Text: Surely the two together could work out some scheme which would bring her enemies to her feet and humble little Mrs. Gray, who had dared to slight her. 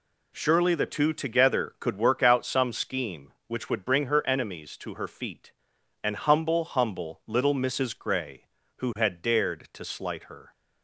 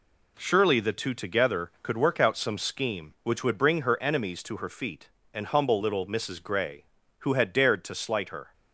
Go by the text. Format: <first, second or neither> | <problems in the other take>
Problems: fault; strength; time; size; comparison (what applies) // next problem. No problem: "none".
second | says "humble" twice; at 6.6 s